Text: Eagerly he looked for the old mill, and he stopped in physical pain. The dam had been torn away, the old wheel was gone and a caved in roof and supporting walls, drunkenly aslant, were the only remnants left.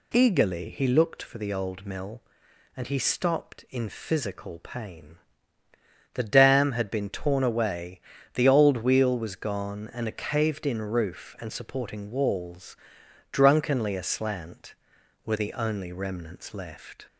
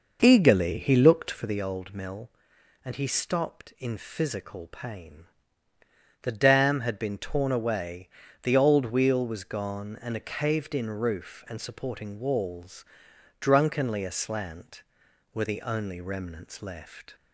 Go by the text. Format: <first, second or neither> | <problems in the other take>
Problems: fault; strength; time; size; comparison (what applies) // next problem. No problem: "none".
first | starts louder than the rest; noticeable; until 1.6 s; 5.5 dB